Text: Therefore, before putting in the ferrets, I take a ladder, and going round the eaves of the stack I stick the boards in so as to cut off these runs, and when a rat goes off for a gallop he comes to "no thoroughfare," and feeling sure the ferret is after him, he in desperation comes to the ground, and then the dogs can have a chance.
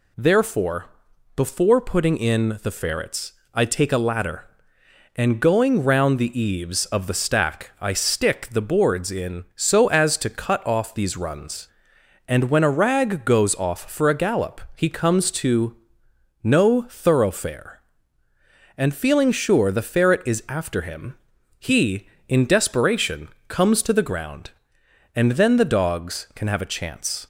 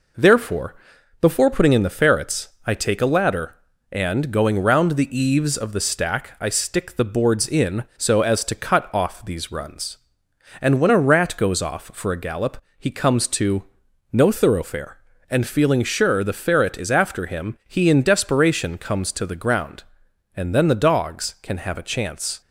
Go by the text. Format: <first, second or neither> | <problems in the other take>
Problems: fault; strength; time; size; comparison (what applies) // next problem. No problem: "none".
second | says "rag" for "rat"; at 12.6 s // pauses between "gallop" and "he"; slight; at 14.5 s; 0.16 s long; slight in the second // pauses between "to" and "no"; noticeable; at 15.7 s; 0.68 s long; noticeable in the second // pauses between "desperation" and "comes"; slight; at 23.2 s; 0.20 s long